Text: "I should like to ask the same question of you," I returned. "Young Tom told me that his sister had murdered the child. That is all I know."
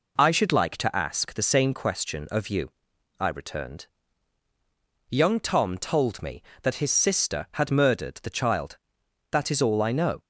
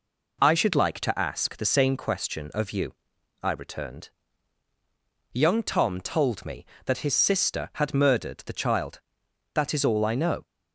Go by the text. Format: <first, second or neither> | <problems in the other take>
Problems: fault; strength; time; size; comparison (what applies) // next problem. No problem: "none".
neither | none